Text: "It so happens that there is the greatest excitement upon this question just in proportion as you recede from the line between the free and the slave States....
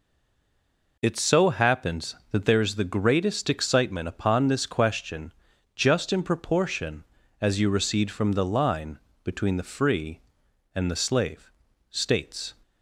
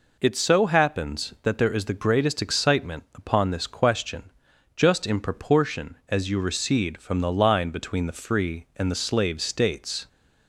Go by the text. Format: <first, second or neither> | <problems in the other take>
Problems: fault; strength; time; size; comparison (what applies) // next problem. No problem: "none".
second | stays silent before the first word; until 0.9 s; 0.9 s long // pauses between "question" and "just"; at 5.3 s; 0.44 s long; also in the second // pauses between "line" and "between"; slight; at 8.9 s; 0.24 s long // pauses between "slave" and "States"; at 11.5 s; 0.40 s long